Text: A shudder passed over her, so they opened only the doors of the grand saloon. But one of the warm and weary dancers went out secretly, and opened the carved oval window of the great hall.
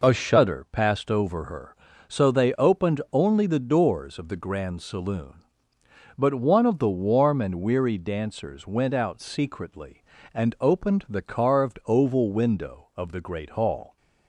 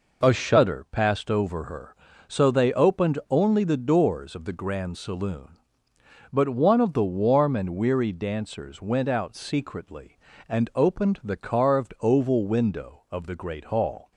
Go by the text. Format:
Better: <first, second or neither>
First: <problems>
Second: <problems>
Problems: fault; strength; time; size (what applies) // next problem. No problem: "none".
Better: neither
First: none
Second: none